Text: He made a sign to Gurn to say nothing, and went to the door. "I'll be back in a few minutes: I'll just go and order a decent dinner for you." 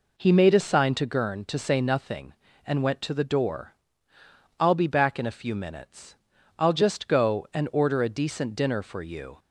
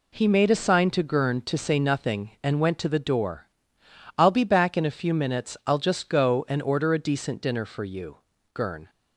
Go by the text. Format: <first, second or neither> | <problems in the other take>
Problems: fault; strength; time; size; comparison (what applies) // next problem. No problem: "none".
first | goes on to say "Gurn"; slight; from 8.5 s on; 0.36 s long